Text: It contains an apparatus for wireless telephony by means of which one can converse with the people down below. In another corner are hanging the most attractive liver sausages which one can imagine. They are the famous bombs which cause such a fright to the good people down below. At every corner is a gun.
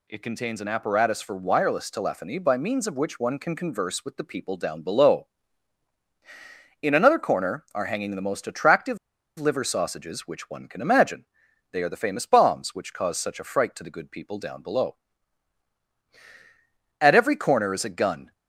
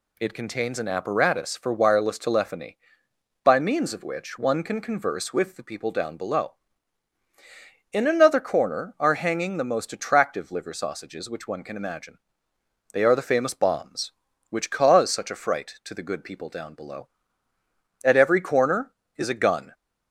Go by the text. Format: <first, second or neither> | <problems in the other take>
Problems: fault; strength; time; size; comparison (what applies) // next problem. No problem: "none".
second | pauses between "attractive" and "liver"; at 8.9 s; 0.42 s long